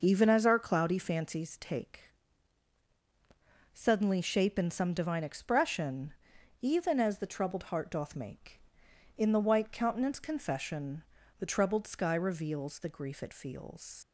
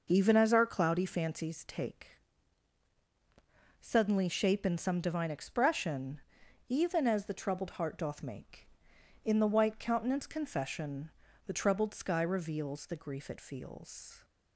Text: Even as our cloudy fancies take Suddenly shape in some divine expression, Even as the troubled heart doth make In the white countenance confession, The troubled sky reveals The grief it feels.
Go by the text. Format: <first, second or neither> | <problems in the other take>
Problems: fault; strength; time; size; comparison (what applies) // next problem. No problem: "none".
second | pauses between "take" and "Suddenly"; strong; at 2.0 s; 1.6 s long; strong in the second // leaves "feels" unfinished; at 14.0 s; 145 ms